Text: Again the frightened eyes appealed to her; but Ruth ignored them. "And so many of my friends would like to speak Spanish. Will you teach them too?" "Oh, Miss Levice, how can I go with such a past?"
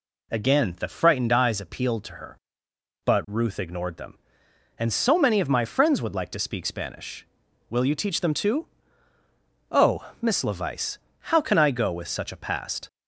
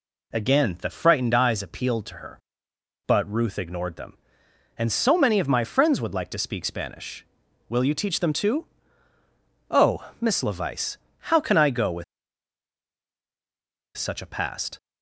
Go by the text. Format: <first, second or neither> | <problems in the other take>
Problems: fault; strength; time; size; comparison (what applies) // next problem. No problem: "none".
first | pauses between "with" and "such"; strong; at 12.0 s; 1.9 s long